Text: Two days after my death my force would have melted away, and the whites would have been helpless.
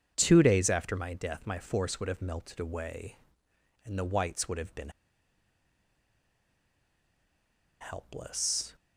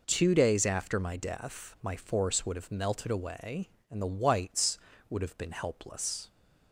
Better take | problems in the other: second | starts louder than the rest; strong; until 1.1 s; 7.5 dB // pauses between "been" and "helpless"; strong; at 4.9 s; 2.9 s long

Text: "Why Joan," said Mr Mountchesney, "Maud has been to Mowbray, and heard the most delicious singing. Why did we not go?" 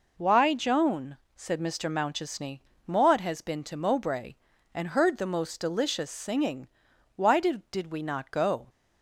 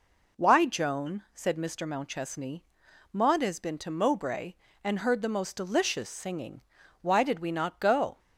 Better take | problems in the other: second | says "did" twice; at 7.7 s

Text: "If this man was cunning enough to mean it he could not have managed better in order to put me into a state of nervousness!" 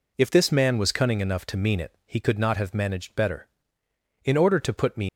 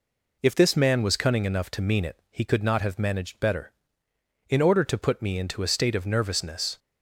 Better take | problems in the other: second | stops before "into a state of nervousness"; at 5.0 s

